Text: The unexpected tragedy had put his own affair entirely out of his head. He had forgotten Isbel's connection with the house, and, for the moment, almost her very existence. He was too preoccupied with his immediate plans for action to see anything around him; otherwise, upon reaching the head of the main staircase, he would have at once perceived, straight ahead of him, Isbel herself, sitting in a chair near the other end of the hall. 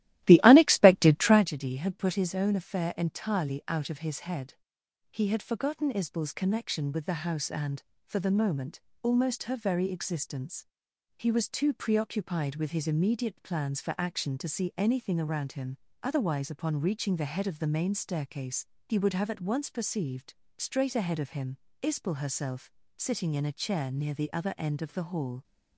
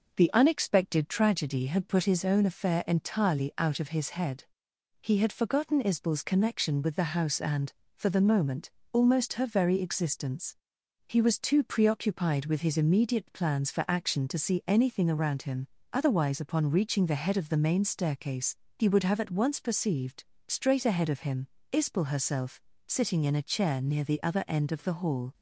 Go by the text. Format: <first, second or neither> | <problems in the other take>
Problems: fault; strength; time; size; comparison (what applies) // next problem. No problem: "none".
second | starts louder than the rest; strong; until 1.5 s; 15 dB